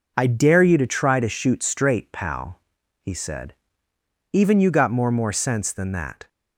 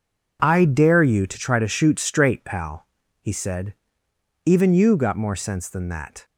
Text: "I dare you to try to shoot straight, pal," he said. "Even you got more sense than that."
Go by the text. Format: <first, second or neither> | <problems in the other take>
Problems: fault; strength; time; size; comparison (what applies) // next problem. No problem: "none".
second | says "more" twice; at 5.0 s